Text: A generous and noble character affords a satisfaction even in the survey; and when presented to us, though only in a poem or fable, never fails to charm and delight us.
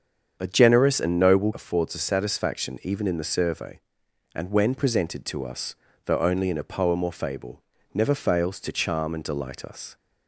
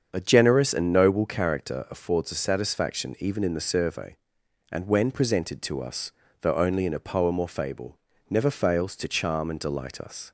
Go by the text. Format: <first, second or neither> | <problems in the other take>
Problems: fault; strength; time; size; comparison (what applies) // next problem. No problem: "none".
second | starts louder than the rest; strong; until 1.4 s; 7.5 dB; also in the second // skips "character"; at 1.5 s